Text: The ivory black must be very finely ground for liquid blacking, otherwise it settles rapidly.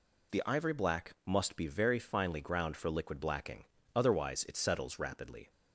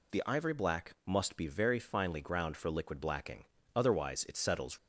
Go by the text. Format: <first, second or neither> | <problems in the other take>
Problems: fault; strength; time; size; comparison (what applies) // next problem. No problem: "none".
first | stops before "rapidly"; at 4.7 s